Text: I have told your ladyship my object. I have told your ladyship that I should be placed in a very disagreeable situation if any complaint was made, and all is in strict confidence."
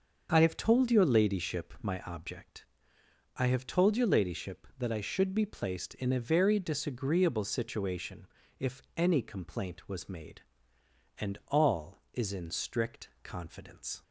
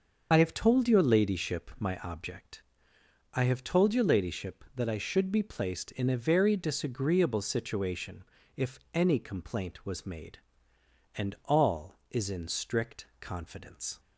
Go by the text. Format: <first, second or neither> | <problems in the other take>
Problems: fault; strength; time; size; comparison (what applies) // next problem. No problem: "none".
first | loses the start of "I"; at 0.3 s; 40 ms // starts louder than the rest; until 1.3 s; 6.5 dB; also in the first // pauses between "situation" and "if"; slight; at 8.2 s; 0.34 s long; slight in the first // pauses between "if" and "any"; slight; at 8.7 s; 0.16 s long; slight in the first // pauses between "strict" and "confidence"; slight; at 13.0 s; 0.16 s long; slight in the first